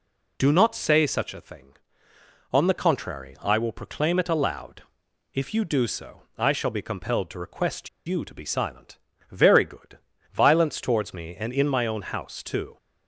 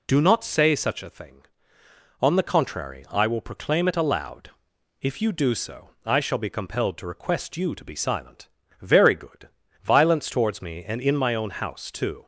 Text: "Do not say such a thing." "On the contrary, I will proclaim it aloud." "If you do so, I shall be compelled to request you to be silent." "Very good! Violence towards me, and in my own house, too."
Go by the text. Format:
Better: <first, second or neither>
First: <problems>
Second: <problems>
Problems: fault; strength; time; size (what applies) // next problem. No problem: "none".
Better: second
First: pauses between "request" and "you"; slight; at 7.8 s; 0.18 s long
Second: none